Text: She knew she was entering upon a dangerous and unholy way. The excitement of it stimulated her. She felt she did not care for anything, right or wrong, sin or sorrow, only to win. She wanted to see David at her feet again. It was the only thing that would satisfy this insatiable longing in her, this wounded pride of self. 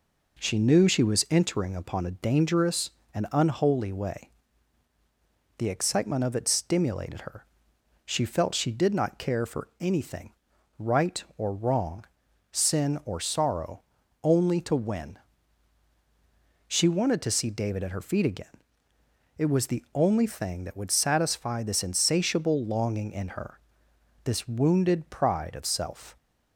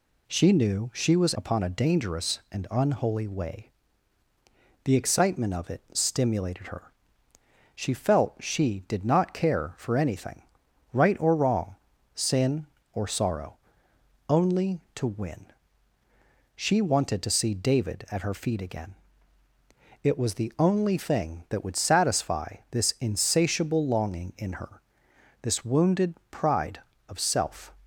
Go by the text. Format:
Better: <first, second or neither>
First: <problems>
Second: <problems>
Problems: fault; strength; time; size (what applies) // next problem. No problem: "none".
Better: first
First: none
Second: skips "entering"; at 1.3 s // pauses between "satisfy" and "this"; slight; at 22.5 s; 0.16 s long // pauses between "wounded" and "pride"; slight; at 26.1 s; 0.16 s long